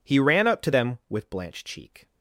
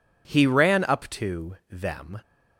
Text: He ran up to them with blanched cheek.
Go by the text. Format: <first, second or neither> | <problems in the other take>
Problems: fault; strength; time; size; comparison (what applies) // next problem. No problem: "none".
first | stops before "with blanched cheek"; at 2.2 s